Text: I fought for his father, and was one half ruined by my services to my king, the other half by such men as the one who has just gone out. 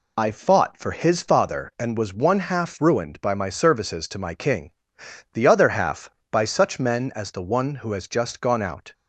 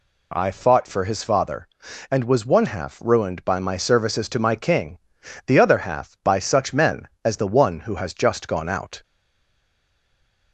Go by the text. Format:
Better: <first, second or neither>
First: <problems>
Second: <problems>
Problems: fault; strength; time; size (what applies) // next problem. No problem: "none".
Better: first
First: none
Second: stays silent after the last word; noticeable; from 9.0 s on; 1.5 s long